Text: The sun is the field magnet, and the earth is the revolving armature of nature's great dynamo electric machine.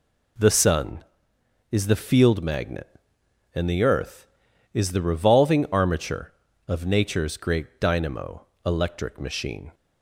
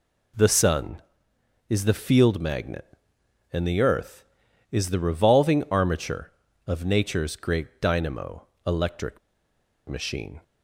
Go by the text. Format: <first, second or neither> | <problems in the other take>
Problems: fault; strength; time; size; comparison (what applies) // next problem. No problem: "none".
first | pauses between "dynamo" and "electric"; slight; at 8.4 s; 0.22 s long; slight in the first // pauses between "electric" and "machine"; noticeable; at 9.1 s; 0.69 s long